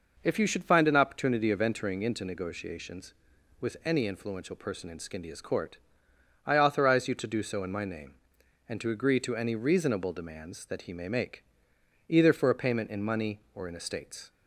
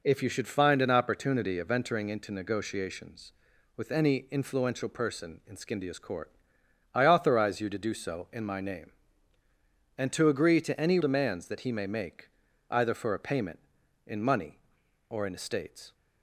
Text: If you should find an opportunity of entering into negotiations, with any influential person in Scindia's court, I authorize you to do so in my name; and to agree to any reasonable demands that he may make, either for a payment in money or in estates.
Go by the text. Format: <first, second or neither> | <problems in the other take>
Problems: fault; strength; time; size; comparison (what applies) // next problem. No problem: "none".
first | skips "reasonable"; at 10.9 s